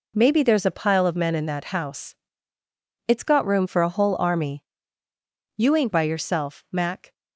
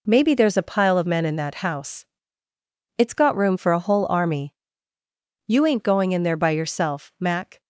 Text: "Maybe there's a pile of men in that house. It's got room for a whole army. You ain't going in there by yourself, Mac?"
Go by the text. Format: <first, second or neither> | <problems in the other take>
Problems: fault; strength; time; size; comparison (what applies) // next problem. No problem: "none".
second | skips "going in there"; at 5.9 s